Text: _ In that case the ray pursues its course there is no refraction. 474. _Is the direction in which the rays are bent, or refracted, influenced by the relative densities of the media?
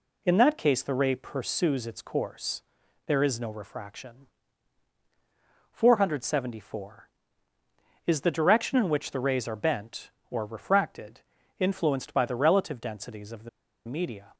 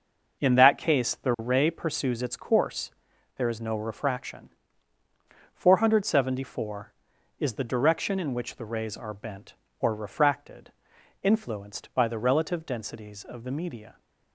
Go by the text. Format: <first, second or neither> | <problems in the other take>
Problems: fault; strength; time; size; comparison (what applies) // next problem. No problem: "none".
second | pauses between "course" and "there"; at 2.6 s; 0.44 s long; noticeable in the second // pauses between "the" and "media"; at 13.4 s; 0.38 s long